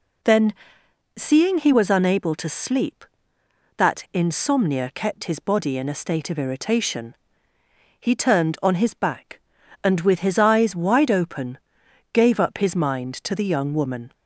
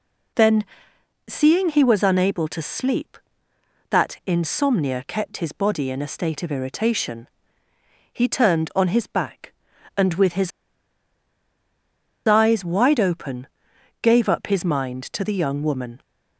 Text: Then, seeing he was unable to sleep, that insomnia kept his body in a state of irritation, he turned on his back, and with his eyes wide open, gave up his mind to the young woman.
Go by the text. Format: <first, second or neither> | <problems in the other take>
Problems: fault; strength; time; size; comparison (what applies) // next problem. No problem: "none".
first | pauses between "his" and "eyes"; strong; at 10.5 s; 1.7 s long